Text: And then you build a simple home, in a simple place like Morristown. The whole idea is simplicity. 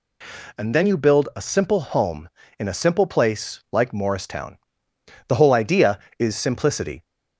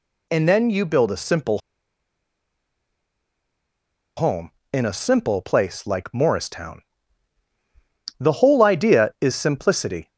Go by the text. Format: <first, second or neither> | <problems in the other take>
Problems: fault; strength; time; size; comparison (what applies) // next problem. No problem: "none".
first | pauses between "simple" and "home"; strong; at 1.5 s; 2.5 s long